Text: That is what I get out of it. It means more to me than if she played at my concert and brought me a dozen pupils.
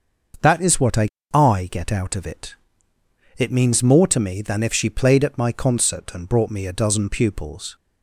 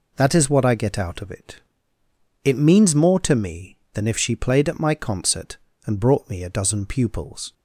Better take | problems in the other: second | starts louder than the rest; until 1.6 s; 6.5 dB // says "I" twice; at 1.3 s

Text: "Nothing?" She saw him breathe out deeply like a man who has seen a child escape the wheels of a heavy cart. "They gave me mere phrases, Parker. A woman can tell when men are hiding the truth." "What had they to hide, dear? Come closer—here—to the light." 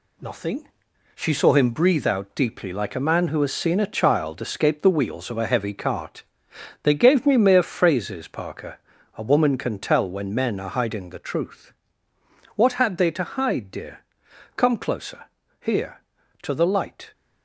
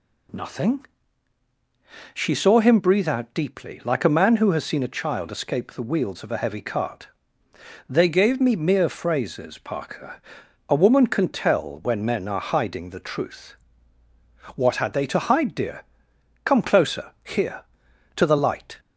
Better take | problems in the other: second | gets quieter; noticeable; throughout; 5 dB

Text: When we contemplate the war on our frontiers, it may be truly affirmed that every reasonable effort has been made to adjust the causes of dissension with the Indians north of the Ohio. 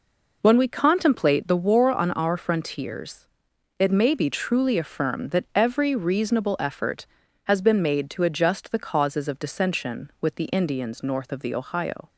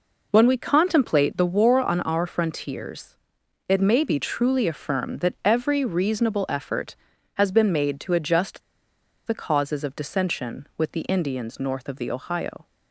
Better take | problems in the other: first | pauses between "adjust" and "the"; noticeable; at 8.6 s; 0.66 s long

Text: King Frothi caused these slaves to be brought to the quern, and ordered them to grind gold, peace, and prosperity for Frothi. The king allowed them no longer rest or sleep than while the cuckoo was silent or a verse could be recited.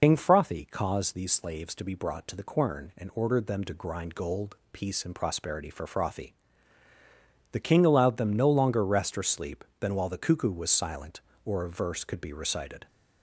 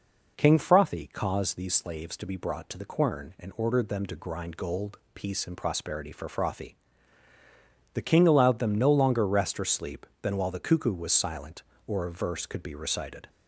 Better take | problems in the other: second | loses the start of "King"; at 0.0 s; 80 ms

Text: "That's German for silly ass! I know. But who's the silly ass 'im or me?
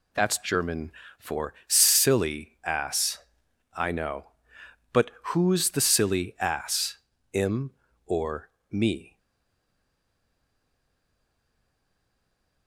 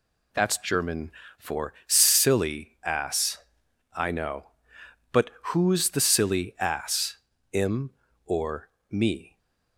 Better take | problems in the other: second | pauses between "But" and "who's"; slight; at 5.0 s; 0.18 s long; slight in the second // pauses between "ass" and "im"; slight; at 6.9 s; 0.34 s long; slight in the second // pauses between "or" and "me"; slight; at 8.4 s; 0.20 s long; slight in the second // stays silent after the last word; strong; from 9.1 s on; 3.5 s long

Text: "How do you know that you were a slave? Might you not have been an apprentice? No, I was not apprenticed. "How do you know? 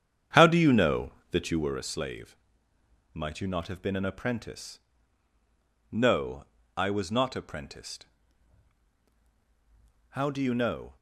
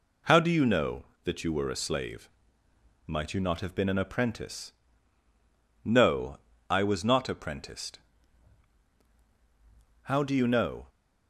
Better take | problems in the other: second | starts louder than the rest; strong; until 1.8 s; 8.5 dB

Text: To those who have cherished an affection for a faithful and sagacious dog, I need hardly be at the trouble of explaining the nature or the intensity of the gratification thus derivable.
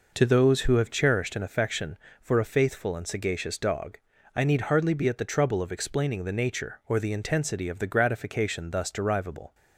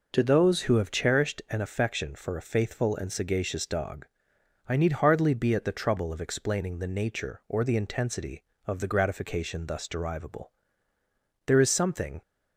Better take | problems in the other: first | goes on to say "There is something"; noticeable; from 11.4 s on; 0.76 s long

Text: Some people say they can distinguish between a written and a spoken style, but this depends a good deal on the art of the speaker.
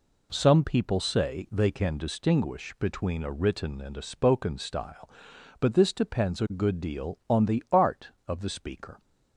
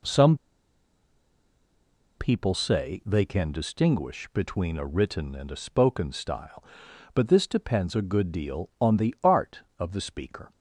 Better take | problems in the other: first | pauses between "Some" and "people"; strong; at 0.3 s; 1.8 s long

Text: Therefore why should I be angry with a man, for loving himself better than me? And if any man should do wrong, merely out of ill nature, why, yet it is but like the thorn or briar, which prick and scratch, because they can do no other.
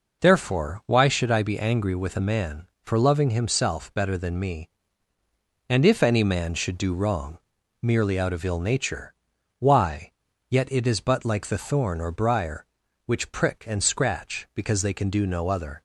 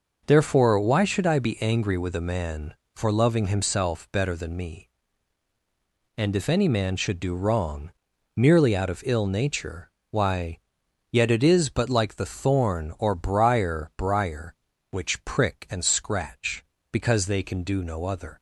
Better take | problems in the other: first | says "briar" twice; at 13.9 s

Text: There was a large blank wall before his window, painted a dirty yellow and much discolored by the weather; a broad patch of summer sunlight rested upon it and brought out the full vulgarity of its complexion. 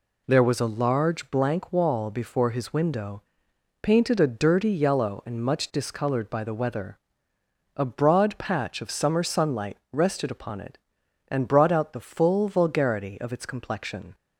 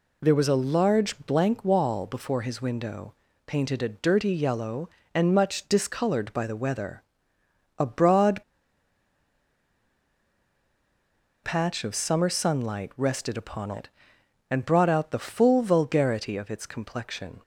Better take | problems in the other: first | pauses between "broad" and "patch"; strong; at 8.4 s; 3.0 s long

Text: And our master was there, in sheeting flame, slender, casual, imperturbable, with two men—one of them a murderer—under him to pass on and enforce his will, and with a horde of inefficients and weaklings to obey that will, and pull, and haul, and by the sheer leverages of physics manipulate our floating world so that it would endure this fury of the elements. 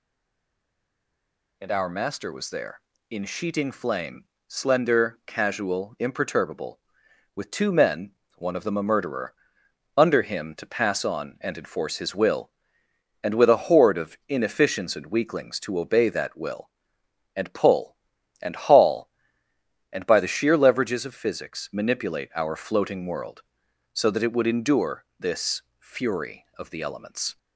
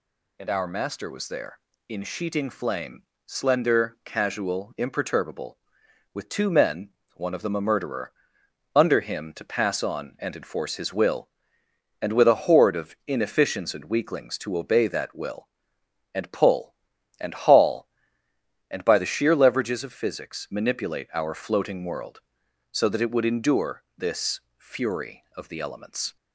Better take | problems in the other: second | stays silent before the first word; noticeable; until 1.5 s; 1.5 s long // pauses between "this" and "fury"; slight; at 25.6 s; 0.18 s long; slight in the second

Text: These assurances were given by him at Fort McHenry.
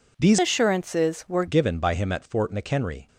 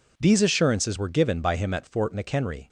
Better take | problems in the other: second | changes voice from "assurances" to "were"; from 0.3 to 1.4 s; 1.1 s long

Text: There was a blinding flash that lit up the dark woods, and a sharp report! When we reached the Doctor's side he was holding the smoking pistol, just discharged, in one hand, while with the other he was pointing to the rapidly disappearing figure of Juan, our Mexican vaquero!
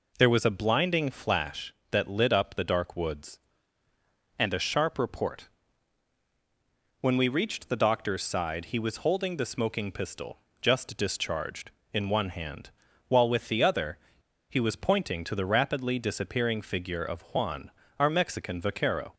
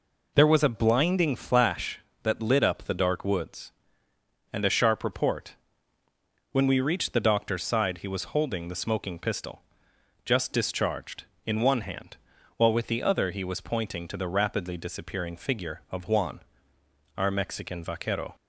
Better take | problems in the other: second | pauses between "other" and "he"; noticeable; at 13.9 s; 0.51 s long

